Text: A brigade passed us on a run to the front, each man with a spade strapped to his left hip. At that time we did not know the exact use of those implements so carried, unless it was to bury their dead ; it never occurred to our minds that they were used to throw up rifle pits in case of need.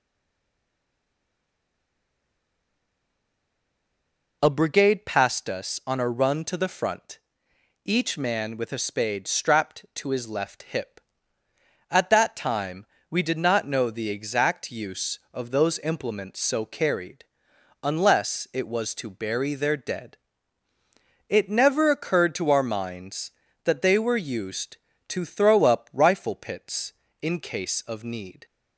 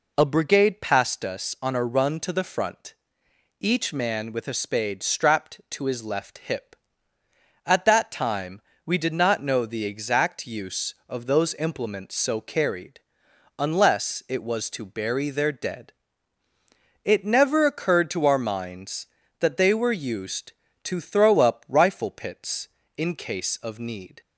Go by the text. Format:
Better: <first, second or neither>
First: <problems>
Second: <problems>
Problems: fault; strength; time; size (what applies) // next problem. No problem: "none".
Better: second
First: stays silent before the first word; strong; until 4.4 s; 4.4 s long // pauses between "time" and "we"; slight; at 12.8 s; 0.24 s long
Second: pauses between "time" and "we"; slight; at 8.6 s; 0.24 s long